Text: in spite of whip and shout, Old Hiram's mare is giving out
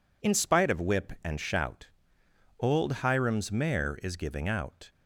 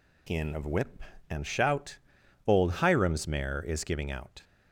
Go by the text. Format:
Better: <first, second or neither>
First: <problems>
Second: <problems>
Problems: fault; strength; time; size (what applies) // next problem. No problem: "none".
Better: first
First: none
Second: skips "spite"; at 0.5 s